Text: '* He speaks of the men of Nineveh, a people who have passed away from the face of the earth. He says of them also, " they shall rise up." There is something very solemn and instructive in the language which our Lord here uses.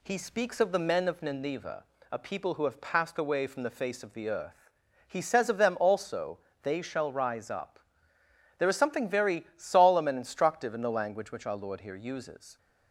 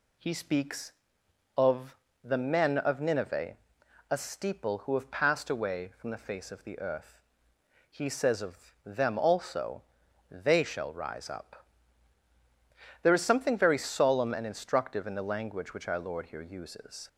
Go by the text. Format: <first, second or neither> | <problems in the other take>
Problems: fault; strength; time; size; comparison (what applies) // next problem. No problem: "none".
first | pauses between "of" and "the"; slight; at 1.9 s; 0.26 s long // says "steeple" for "people"; at 4.1 s